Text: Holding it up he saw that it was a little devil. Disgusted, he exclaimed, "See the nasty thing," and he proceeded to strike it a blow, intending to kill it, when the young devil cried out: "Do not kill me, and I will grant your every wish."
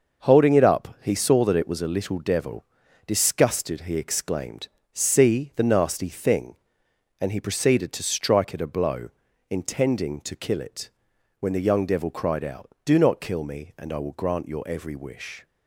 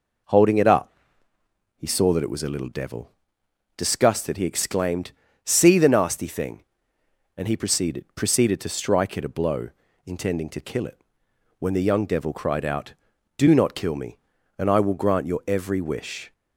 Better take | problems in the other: first | pauses between "up" and "he"; noticeable; at 0.9 s; 0.86 s long // says "proceeded" twice; at 8.1 s

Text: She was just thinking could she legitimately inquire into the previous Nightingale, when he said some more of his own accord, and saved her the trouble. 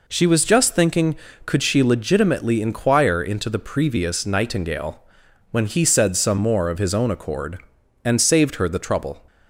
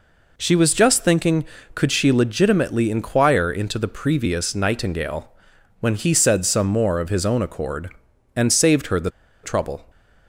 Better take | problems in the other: first | pauses between "the" and "trouble"; slight; at 9.1 s; 0.32 s long

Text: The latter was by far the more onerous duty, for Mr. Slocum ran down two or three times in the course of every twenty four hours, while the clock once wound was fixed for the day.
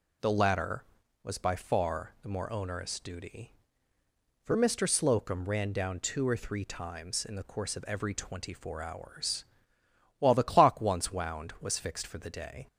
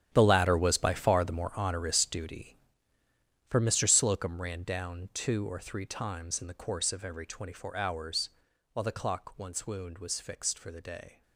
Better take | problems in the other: first | gets quieter; strong; throughout; 15.5 dB

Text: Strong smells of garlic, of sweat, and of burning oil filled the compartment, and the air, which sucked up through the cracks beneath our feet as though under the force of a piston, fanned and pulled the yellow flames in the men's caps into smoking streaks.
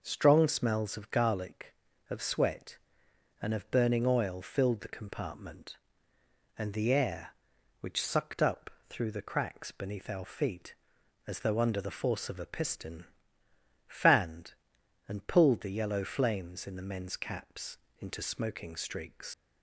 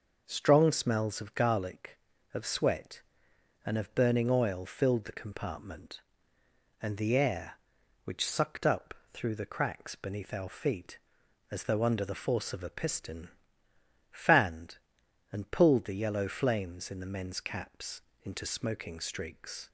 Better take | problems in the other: second | pauses between "up" and "through"; slight; at 8.6 s; 0.18 s long; slight in the second // pauses between "caps" and "into"; slight; at 17.7 s; 0.22 s long; slight in the second // leaves "streaks" unfinished; at 19.3 s; 115 ms

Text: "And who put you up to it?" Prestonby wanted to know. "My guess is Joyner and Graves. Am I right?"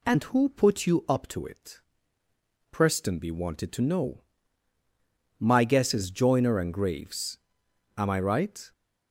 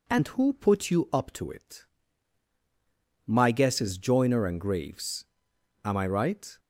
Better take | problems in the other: first | skips "Prestonby wanted to know"; at 2.5 s

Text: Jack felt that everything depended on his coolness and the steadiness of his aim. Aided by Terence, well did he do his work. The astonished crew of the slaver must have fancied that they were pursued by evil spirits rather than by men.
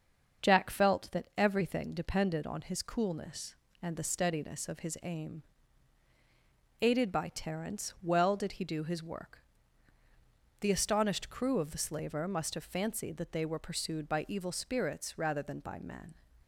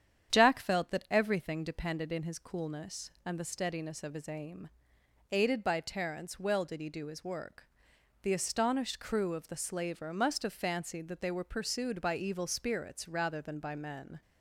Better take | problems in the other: first | starts louder than the rest; strong; until 1.3 s; 9 dB; also in the first // says "in" for "on"; at 2.1 s

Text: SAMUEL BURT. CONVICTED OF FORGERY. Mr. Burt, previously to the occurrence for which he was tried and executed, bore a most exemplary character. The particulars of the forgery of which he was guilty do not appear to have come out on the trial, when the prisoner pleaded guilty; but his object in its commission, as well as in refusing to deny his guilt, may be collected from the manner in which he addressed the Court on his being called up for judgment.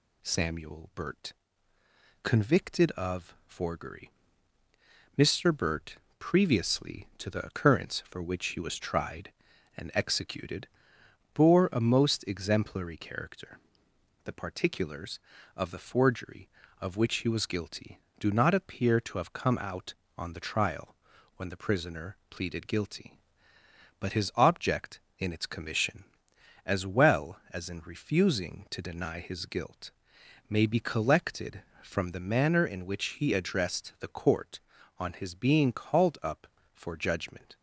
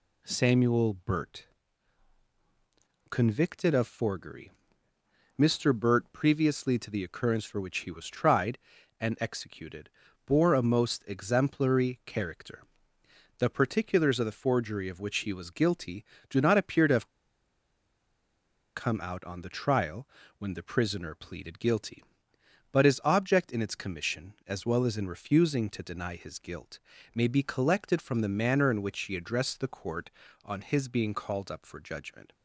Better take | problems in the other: first | pauses between "have" and "come"; strong; at 17.0 s; 1.6 s long

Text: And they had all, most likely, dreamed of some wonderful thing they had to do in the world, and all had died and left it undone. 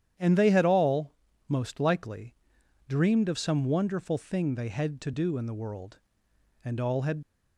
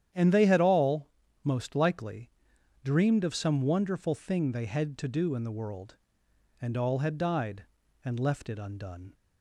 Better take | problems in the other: second | starts louder than the rest; strong; until 1.5 s; 10 dB; strong in the second // stops before "died and left it undone"; at 7.2 s

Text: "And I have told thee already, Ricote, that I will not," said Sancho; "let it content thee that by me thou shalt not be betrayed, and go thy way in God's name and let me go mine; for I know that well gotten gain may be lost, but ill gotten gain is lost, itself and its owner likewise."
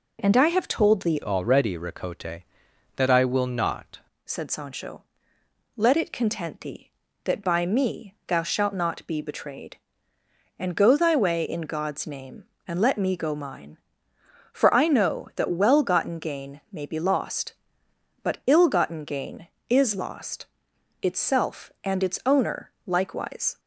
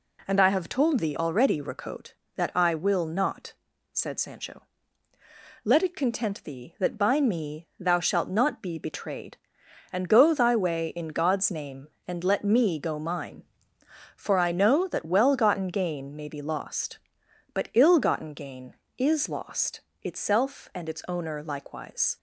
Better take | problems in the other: second | changes voice from "already" to "not"; from 1.2 to 3.9 s; 2.7 s long // pauses between "owner" and "likewise"; slight; at 22.6 s; 0.16 s long

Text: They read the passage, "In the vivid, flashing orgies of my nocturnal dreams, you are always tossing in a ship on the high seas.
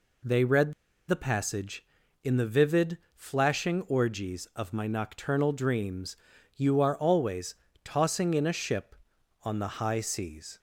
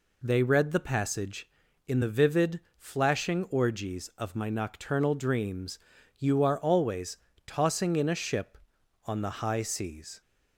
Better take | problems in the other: second | pauses between "read" and "the"; at 0.7 s; 0.36 s long // pauses between "always" and "tossing"; slight; at 7.5 s; 0.30 s long; slight in the second

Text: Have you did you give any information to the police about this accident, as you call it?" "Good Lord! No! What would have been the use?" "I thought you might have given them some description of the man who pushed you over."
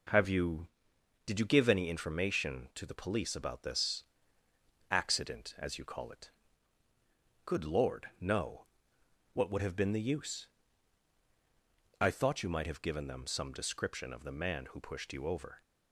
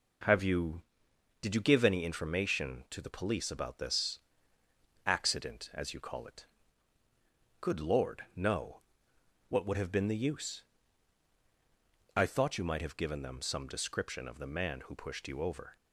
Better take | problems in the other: neither | pauses between "this" and "accident"; noticeable; the same in both

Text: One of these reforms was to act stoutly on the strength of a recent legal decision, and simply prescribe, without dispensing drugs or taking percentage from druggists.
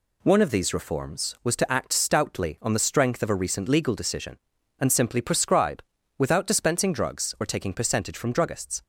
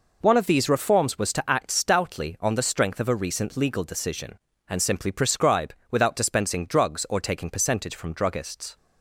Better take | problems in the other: neither | none

